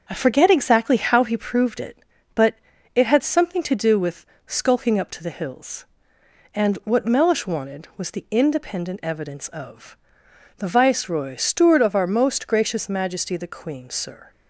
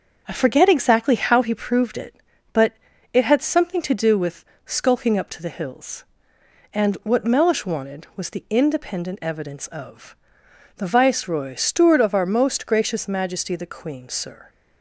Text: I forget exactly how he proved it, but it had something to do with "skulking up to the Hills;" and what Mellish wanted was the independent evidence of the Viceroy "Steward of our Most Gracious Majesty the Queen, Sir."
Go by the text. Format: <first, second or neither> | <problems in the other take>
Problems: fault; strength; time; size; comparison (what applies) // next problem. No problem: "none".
neither | starts louder than the rest; the same in both // pauses between "but" and "it"; the same in both // pauses between "with" and "skulking"; slight; the same in both // pauses between "of" and "the"; noticeable; the same in both